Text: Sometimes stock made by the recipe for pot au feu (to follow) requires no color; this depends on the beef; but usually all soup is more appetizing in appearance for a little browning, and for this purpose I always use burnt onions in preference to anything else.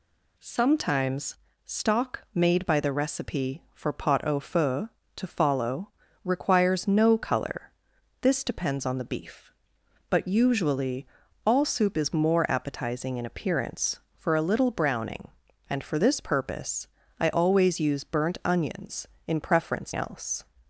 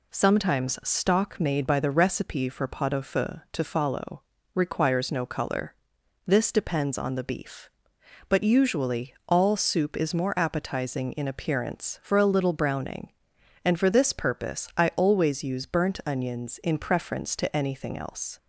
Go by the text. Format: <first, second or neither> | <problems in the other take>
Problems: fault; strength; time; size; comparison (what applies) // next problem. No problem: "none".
second | pauses between "Sometimes" and "stock"; slight; at 1.3 s; 0.30 s long // pauses between "usually" and "all"; at 11.0 s; 0.40 s long // pauses between "purpose" and "I"; slight; at 16.8 s; 0.32 s long // skips "to anything"; at 19.9 s